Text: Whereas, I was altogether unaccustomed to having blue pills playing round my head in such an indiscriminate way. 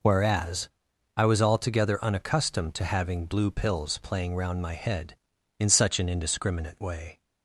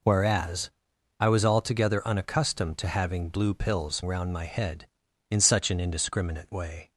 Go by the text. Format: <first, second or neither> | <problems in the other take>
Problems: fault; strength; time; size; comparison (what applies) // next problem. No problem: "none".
first | skips "playing"; at 4.0 s